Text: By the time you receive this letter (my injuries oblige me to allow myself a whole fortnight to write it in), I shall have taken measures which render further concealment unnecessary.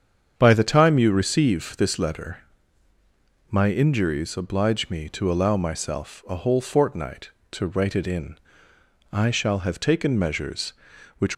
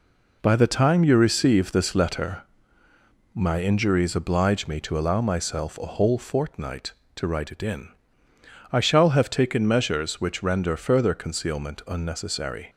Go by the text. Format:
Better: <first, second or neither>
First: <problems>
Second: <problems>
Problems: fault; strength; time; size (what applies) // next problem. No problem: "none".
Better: second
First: starts louder than the rest; strong; until 1.3 s; 7.5 dB // stops before "render further concealment unnecessary"; at 11.3 s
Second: none